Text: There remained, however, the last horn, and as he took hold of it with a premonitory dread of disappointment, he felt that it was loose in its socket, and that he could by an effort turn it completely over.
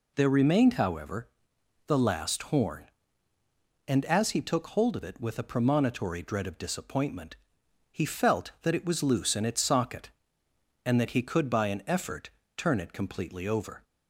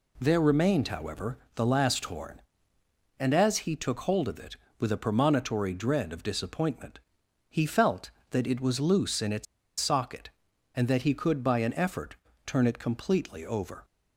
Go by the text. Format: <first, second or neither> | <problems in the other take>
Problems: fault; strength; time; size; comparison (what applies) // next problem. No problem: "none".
first | pauses between "its" and "socket"; slight; at 9.4 s; 0.35 s long // pauses between "effort" and "turn"; slight; at 12.1 s; 0.32 s long; slight in the first